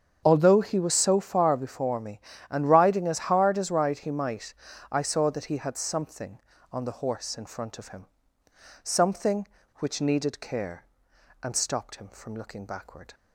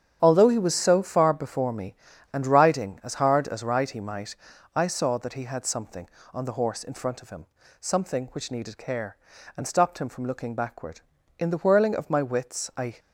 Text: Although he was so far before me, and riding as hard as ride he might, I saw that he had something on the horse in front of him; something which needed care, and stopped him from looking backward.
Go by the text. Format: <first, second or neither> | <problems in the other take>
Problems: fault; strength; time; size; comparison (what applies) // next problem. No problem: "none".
first | starts louder than the rest; strong; until 1.2 s; 8.5 dB; strong in the first // goes on to say "In the whirling of my wits I"; from 11.4 s on; 1.5 s long